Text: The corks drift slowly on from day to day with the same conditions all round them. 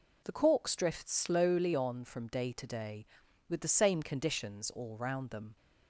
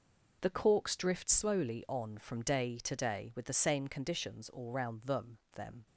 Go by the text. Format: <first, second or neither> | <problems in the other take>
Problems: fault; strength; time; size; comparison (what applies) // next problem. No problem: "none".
first | says "them" twice; at 5.5 s